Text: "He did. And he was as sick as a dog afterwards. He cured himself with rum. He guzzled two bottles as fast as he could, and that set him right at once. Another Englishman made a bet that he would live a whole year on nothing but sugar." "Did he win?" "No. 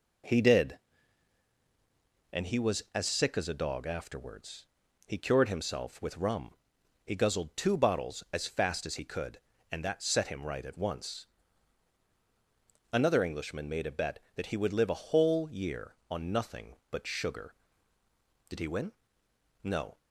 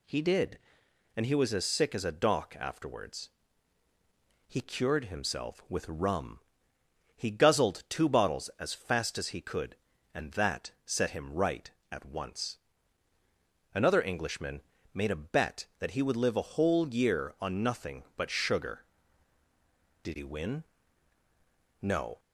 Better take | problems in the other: first | says "dock" for "dog"; at 2.1 s // pauses between "Englishman" and "made"; slight; at 14.6 s; 0.30 s long

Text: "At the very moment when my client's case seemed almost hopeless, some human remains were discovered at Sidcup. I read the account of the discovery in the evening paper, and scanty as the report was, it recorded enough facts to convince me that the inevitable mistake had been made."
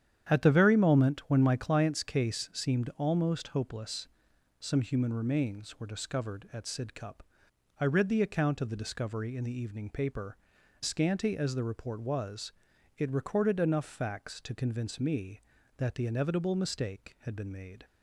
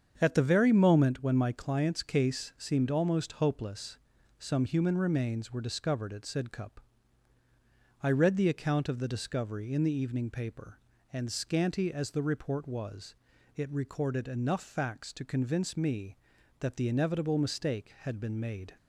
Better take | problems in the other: second | starts louder than the rest; strong; until 1.3 s; 9.5 dB; strong in the second // skips "and"; at 10.5 s

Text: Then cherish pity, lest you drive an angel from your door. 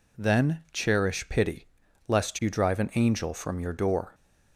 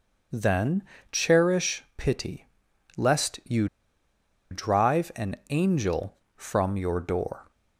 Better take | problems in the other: first | starts louder than the rest; until 1.6 s; 6.5 dB // pauses between "Then" and "cherish"; slight; at 0.8 s; 0.28 s long // pauses between "you" and "drive"; noticeable; at 3.6 s; 0.84 s long

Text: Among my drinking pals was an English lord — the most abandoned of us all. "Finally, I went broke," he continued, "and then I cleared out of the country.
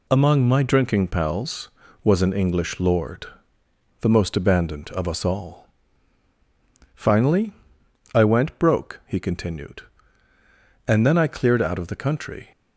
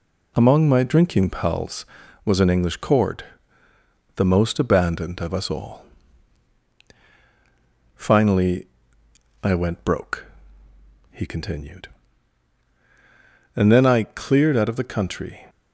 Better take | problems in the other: first | says "cord" for "lord"; at 2.7 s

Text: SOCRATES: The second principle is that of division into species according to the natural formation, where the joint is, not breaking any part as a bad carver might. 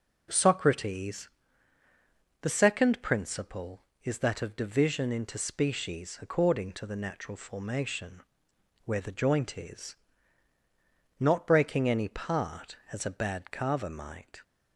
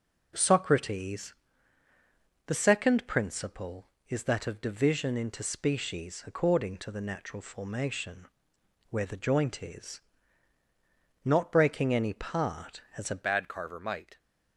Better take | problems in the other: first | changes voice at "bad"; from 13.2 s on; 0.9 s long

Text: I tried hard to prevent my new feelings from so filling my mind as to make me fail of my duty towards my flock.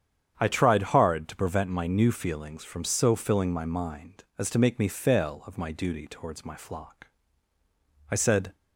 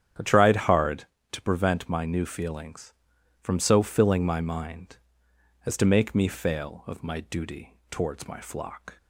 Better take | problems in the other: second | starts louder than the rest; strong; until 1.3 s; 8.5 dB; strong in the second // goes on to say "I said"; slight; from 8.0 s on; 0.46 s long

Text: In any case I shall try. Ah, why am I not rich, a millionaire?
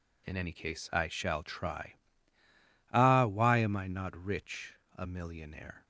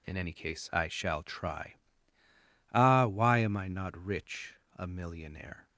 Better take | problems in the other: neither | none

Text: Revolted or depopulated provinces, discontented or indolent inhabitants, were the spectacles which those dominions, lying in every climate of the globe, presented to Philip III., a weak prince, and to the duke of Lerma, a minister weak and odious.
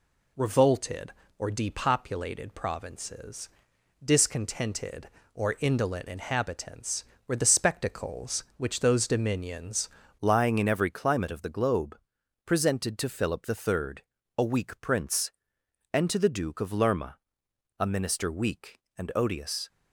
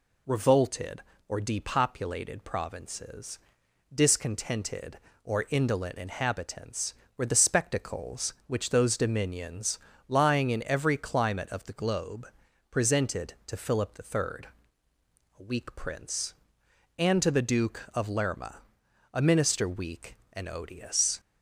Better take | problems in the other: second | changes voice at "lying"; from 10.2 s on; 9.4 s long

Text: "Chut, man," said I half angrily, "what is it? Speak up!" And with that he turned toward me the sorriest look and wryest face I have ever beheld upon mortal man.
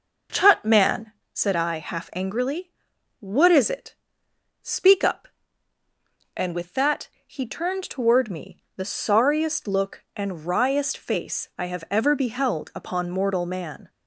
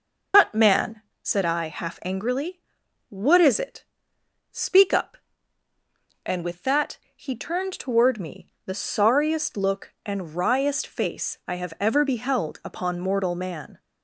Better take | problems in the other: first | loses the start of "Chut"; at 0.3 s; 150 ms // pauses between "that" and "he"; slight; at 6.9 s; 0.18 s long; slight in the first // pauses between "me" and "the"; slight; at 8.5 s; 0.16 s long; slight in the first

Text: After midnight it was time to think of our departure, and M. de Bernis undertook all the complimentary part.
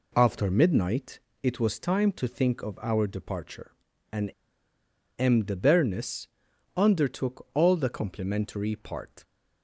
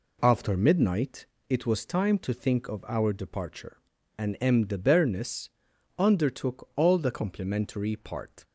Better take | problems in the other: second | pauses between "midnight" and "it"; slight; at 1.1 s; 0.22 s long; slight in the second // pauses between "and" and "M"; noticeable; at 4.2 s; 0.89 s long // pauses between "Bernis" and "undertook"; noticeable; at 6.2 s; 0.48 s long; noticeable in the second

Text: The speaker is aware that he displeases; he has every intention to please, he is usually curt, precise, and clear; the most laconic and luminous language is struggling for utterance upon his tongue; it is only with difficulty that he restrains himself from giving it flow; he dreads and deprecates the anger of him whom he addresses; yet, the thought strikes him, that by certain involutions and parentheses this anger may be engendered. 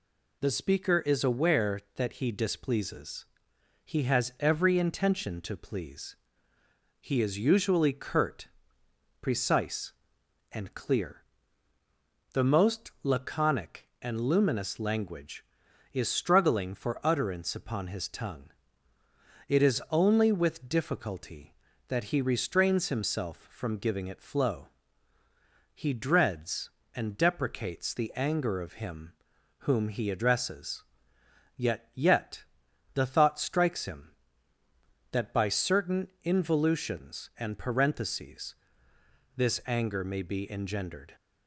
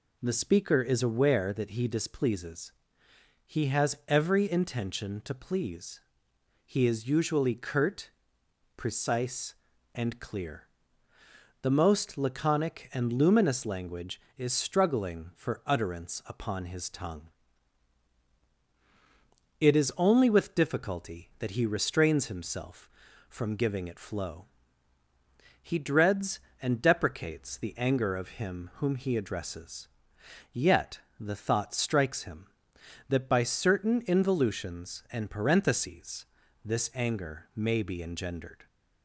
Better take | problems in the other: second | pauses between "him" and "whom"; noticeable; at 29.1 s; 0.46 s long // says "yet" twice; at 31.9 s // pauses between "certain" and "involutions"; slight; at 36.0 s; 0.16 s long // pauses between "parentheses" and "this"; noticeable; at 38.5 s; 0.82 s long; also in the second

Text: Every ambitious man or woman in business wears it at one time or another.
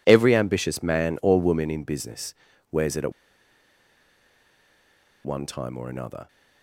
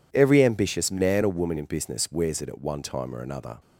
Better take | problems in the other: second | pauses between "business" and "wears"; at 2.3 s; 0.38 s long // pauses between "at" and "one"; strong; at 3.1 s; 2.1 s long

